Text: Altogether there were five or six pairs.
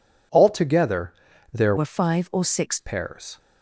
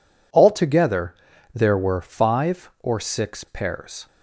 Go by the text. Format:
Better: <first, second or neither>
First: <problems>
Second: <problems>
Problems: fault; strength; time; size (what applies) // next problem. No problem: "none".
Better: second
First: pauses between "Altogether" and "there"; at 1.1 s; 0.40 s long // changes voice from "were" to "six"; from 1.7 to 2.7 s; 1.0 s long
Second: pauses between "Altogether" and "there"; at 1.1 s; 0.40 s long